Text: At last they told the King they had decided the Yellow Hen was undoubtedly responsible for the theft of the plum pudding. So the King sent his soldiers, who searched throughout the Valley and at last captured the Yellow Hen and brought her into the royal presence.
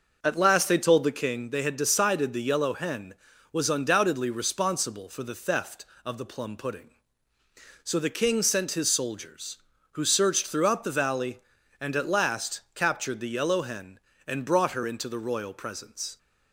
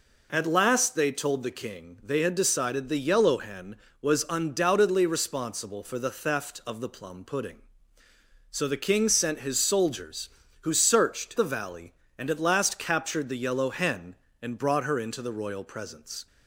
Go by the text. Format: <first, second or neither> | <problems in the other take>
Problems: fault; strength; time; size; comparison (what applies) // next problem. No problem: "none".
first | skips "throughout"; at 11.3 s